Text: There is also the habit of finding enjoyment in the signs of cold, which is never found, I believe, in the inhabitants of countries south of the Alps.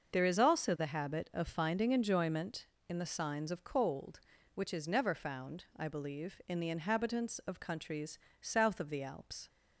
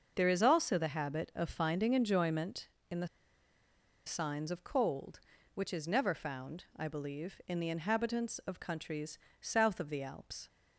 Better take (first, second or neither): first